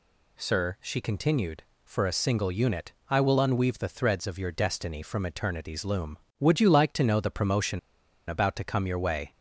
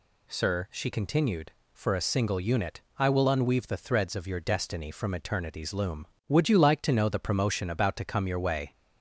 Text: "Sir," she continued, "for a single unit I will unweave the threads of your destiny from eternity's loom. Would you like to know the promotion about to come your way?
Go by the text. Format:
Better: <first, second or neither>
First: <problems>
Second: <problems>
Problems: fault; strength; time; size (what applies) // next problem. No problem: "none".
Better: second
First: pauses between "unit" and "I"; slight; at 2.9 s; 0.18 s long // pauses between "promotion" and "about"; noticeable; at 7.7 s; 0.48 s long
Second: pauses between "unit" and "I"; slight; at 2.8 s; 0.18 s long